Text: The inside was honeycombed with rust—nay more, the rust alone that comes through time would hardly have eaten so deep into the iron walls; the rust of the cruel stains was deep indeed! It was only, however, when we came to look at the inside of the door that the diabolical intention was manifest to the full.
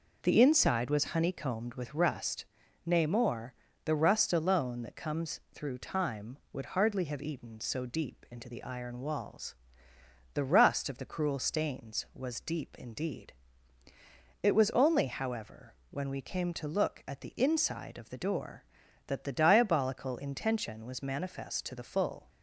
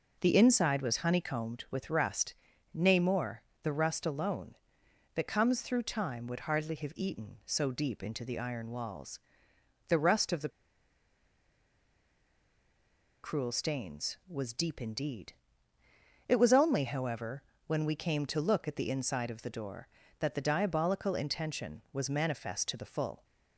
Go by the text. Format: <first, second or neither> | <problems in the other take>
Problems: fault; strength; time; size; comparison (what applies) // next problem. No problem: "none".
first | pauses between "the" and "cruel"; strong; at 10.4 s; 2.7 s long